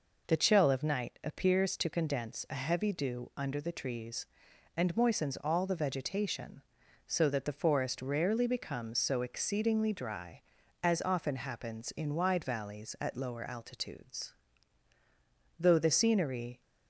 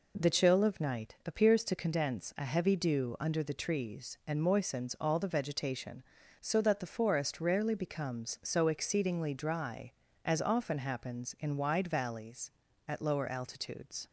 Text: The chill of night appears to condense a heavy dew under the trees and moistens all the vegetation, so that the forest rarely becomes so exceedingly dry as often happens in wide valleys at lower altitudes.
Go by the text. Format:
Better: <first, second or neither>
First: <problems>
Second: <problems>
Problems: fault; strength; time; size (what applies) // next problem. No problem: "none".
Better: second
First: goes on to say "Though the scenery"; noticeable; from 15.5 s on; 1.0 s long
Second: none